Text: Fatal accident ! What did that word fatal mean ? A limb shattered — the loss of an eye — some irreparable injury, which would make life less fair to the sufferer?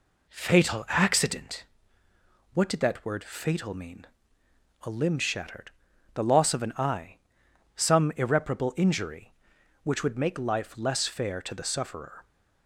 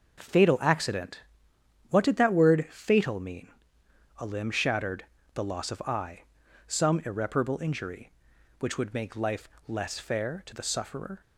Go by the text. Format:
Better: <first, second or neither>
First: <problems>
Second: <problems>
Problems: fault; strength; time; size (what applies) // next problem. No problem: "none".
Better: first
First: none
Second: starts louder than the rest; noticeable; until 1.9 s; 6 dB // skips "an"; at 5.8 s // pauses between "life" and "less"; slight; at 9.4 s; 0.18 s long